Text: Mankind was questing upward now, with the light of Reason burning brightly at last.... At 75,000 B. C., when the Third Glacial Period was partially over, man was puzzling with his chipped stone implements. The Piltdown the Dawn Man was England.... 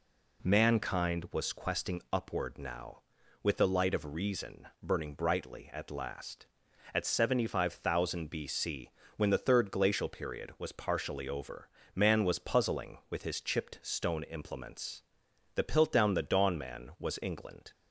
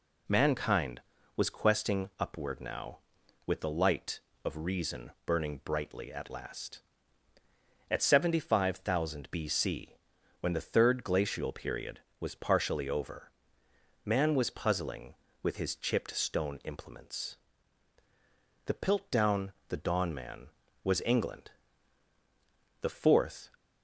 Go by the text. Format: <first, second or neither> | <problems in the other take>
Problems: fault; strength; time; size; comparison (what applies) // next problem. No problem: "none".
first | pauses between "Piltdown" and "the"; slight; at 19.5 s; 0.18 s long // goes on to say "The Fourth"; noticeable; from 22.8 s on; 0.70 s long